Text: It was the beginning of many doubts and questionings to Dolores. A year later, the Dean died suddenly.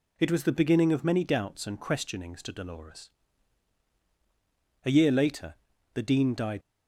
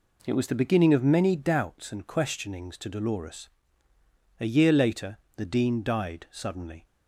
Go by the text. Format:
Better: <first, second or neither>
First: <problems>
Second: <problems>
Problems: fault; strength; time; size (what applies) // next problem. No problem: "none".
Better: second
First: stops before "suddenly"; at 6.6 s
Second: none